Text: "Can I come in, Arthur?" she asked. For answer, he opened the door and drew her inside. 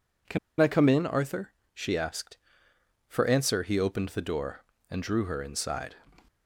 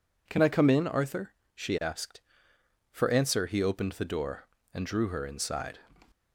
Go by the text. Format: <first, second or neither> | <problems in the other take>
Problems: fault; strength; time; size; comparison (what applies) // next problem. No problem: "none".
second | pauses between "Can" and "I"; slight; at 0.3 s; 0.22 s long